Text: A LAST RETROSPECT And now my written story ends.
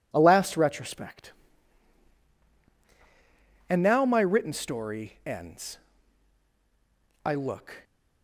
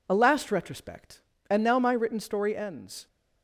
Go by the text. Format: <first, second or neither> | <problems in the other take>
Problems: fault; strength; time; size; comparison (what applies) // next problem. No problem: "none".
second | goes on to say "I look"; from 7.2 s on; 0.60 s long